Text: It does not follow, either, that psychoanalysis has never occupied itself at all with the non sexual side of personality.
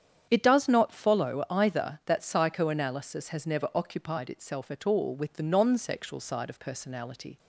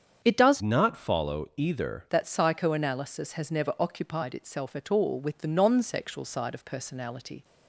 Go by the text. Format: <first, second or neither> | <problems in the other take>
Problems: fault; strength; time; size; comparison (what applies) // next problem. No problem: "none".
first | starts louder than the rest; strong; until 1.2 s; 7.5 dB; strong in the first // changes voice from "not" to "either"; from 0.6 to 2.0 s; 1.4 s long